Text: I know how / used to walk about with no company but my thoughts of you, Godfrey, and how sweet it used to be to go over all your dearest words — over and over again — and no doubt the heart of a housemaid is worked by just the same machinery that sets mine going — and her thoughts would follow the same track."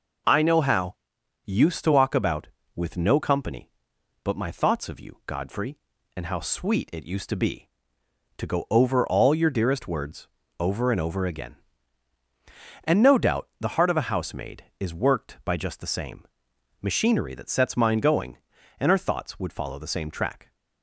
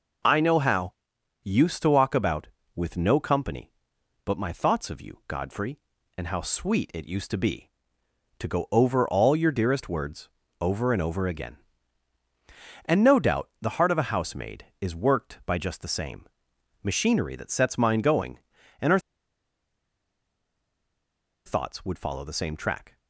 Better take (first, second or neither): first